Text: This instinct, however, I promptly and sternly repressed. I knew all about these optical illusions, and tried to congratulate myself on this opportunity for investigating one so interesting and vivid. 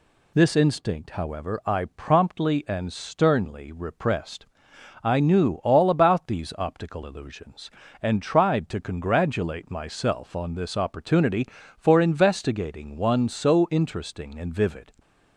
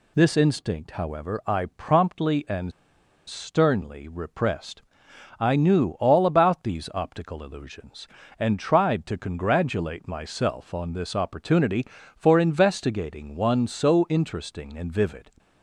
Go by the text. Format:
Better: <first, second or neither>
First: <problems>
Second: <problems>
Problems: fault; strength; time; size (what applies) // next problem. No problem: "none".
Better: first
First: none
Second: pauses between "and" and "sternly"; noticeable; at 2.7 s; 0.56 s long